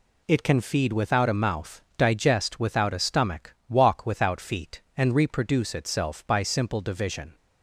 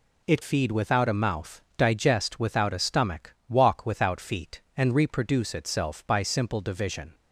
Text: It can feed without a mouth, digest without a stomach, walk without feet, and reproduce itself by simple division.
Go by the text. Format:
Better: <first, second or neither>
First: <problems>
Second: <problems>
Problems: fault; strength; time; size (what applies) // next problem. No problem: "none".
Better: first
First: none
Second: skips "can"; at 0.4 s